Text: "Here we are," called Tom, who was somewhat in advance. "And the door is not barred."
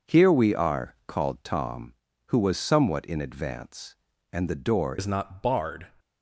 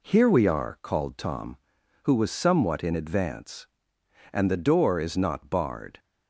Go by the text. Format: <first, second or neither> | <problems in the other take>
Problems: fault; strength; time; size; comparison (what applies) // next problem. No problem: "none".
second | changes voice at "is"; from 4.9 s on; 0.9 s long